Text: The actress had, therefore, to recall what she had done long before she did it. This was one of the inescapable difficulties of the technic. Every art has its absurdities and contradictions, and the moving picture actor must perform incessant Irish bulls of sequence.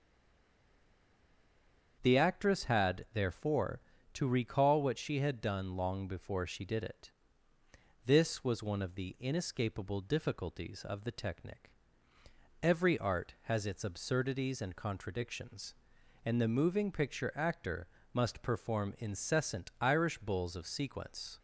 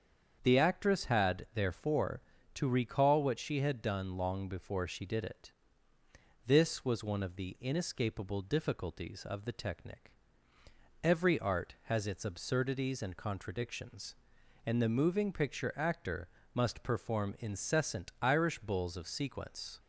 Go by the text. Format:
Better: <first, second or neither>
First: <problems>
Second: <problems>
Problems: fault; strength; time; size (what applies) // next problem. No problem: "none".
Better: second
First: stays silent before the first word; noticeable; until 2.0 s; 2.0 s long // starts louder than the rest; strong; until 3.0 s; 7.5 dB // pauses between "actor" and "must"; slight; at 17.8 s; 0.24 s long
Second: starts louder than the rest; strong; until 1.4 s; 7.5 dB // pauses between "actor" and "must"; slight; at 16.2 s; 0.24 s long